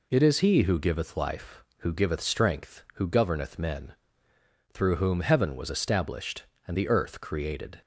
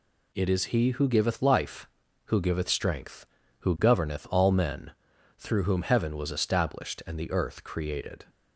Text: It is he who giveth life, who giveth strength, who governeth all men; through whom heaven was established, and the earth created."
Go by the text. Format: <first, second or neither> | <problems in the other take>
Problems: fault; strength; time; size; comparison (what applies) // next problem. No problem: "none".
second | skips "all"; at 3.5 s